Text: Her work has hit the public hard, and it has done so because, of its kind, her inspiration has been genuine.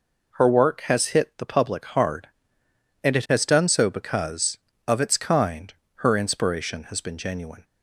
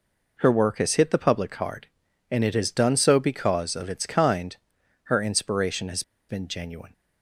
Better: first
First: none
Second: pauses between "has" and "been"; slight; at 6.0 s; 0.27 s long

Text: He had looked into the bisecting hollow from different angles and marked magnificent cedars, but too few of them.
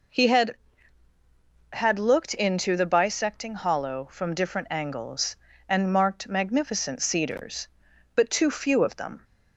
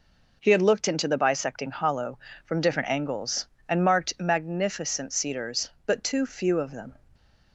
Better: second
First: says "had" twice; at 1.7 s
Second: none

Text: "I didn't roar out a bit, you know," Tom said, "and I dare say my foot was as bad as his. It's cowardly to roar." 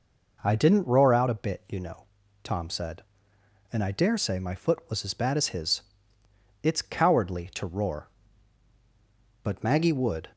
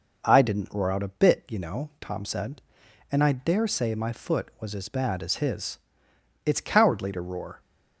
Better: second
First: goes on to say "But Maggie would"; noticeable; from 9.4 s on; 0.86 s long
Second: none

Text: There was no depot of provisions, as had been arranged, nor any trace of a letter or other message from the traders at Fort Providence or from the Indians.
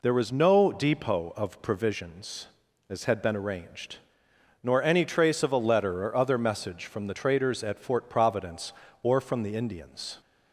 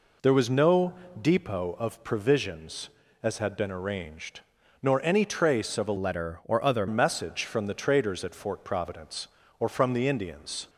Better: first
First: none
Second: pauses between "no" and "depot"; slight; at 0.9 s; 0.26 s long // changes voice from "letter" to "other"; from 5.9 to 6.8 s; 0.9 s long

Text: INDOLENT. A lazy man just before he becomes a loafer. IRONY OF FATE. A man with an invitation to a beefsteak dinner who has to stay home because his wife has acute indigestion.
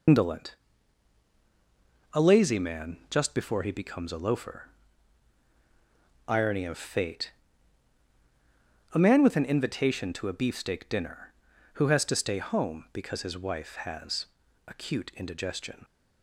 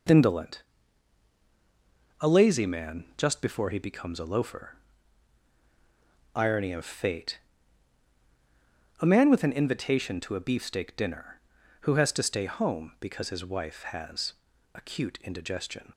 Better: second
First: loses the start of "INDOLENT"; at 0.0 s; 85 ms // pauses between "has" and "acute"; at 14.2 s; 0.40 s long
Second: pauses between "has" and "acute"; at 14.3 s; 0.40 s long

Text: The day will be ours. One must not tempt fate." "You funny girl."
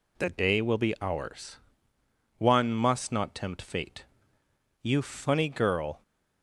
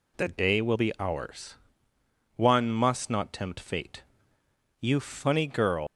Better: first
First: none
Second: leaves "girl" unfinished; at 5.8 s; 130 ms

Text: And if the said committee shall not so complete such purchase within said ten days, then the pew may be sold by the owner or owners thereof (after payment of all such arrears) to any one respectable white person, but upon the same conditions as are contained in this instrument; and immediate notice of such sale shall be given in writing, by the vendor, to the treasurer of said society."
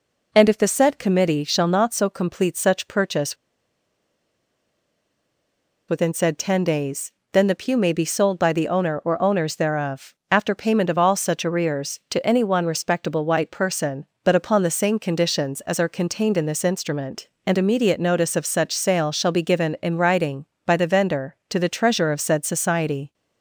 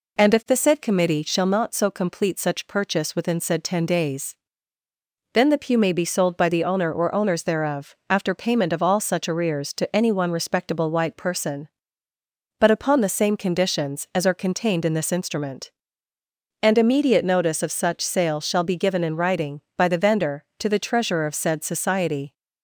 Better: second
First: pauses between "purchase" and "within"; strong; at 3.3 s; 2.5 s long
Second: none

